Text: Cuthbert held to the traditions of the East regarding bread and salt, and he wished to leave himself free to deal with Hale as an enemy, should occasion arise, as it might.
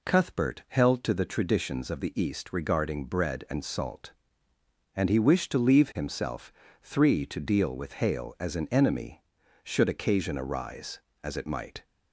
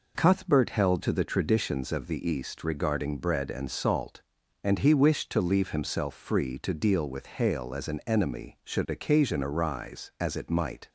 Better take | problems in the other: second | says "three" for "free"; at 6.8 s

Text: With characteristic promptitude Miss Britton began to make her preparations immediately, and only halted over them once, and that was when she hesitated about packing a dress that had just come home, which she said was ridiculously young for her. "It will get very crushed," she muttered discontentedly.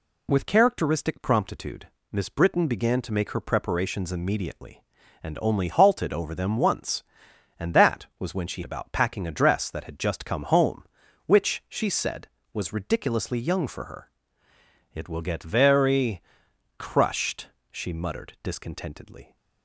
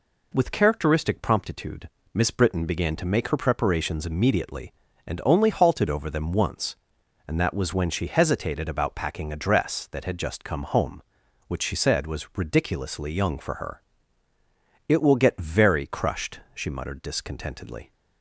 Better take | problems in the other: second | pauses between "promptitude" and "Miss"; slight; at 1.8 s; 0.24 s long; slight in the second // skips "hesitated"; at 8.6 s // pauses between "very" and "crushed"; noticeable; at 16.1 s; 0.56 s long

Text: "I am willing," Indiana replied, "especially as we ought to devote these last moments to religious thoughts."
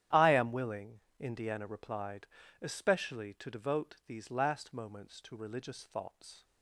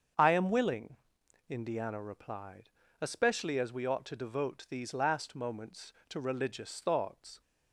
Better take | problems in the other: second | starts louder than the rest; strong; until 1.3 s; 11 dB; strong in the second // skips "as we ought"; at 3.3 s

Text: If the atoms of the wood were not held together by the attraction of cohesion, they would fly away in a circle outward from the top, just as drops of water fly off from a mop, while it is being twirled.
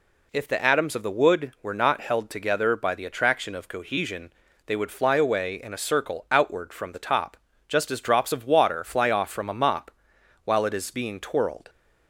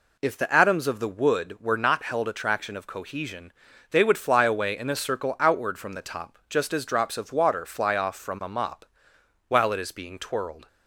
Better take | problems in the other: first | skips "together by the"; at 2.2 s

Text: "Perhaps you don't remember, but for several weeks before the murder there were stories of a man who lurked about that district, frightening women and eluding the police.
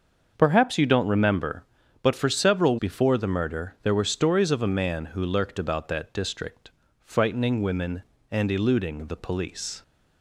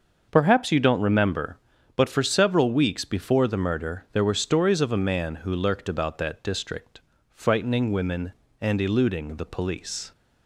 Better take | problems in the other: second | starts louder than the rest; until 1.3 s; 6.5 dB; also in the second // skips "weeks"; at 2.7 s

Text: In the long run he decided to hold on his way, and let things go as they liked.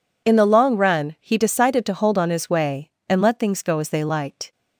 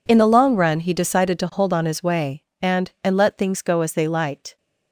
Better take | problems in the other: first | says "and" twice; at 3.0 s

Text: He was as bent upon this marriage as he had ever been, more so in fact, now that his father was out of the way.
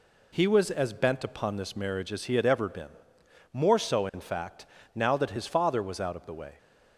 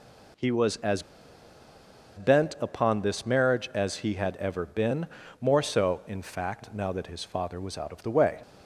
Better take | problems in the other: first | pauses between "as" and "bent"; at 1.0 s; 1.1 s long

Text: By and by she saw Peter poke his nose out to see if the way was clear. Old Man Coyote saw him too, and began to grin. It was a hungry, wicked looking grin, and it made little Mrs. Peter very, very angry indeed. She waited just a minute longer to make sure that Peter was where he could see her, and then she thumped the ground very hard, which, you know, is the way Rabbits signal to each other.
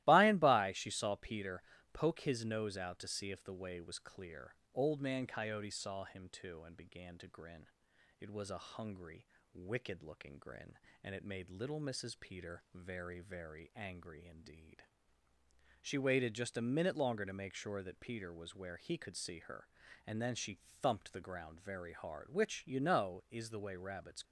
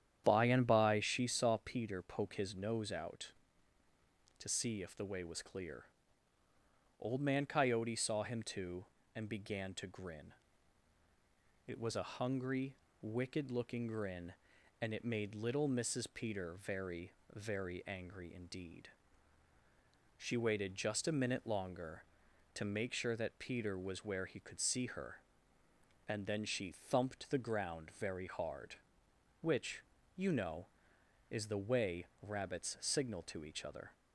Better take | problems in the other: second | starts louder than the rest; strong; until 1.0 s; 16.5 dB; strong in the second // pauses between "Peter" and "poke"; slight; at 1.6 s; 0.30 s long // pauses between "she" and "thumped"; slight; at 20.6 s; 0.20 s long // stops before "signal to each other"; at 24.2 s

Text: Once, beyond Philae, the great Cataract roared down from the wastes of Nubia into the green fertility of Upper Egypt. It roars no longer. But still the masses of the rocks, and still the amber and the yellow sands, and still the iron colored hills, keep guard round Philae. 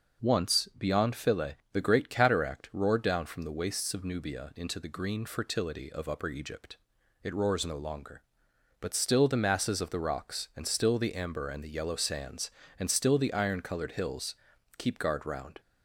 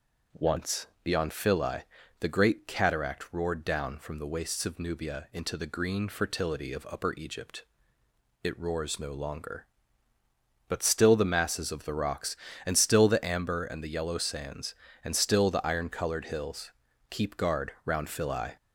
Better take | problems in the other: second | stops before "Philae"; at 15.6 s

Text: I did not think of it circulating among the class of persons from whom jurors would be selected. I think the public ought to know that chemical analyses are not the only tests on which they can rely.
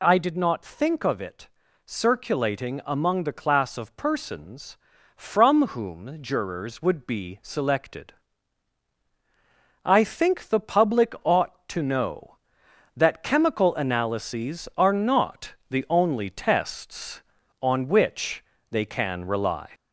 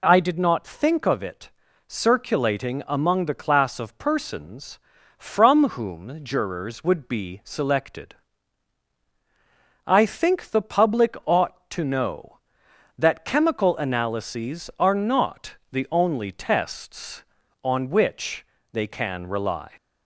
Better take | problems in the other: second | gets louder; slight; throughout; 3 dB // pauses between "it" and "circulating"; at 1.4 s; 0.38 s long; also in the second // pauses between "not" and "the"; slight; at 15.5 s; 0.16 s long; slight in the second // pauses between "which" and "they"; slight; at 18.4 s; 0.26 s long; slight in the second

